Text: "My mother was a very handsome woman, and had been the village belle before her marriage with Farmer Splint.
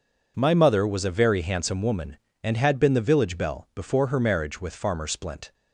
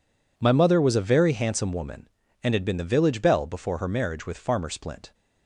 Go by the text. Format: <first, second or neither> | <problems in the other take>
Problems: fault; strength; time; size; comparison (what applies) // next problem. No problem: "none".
neither | none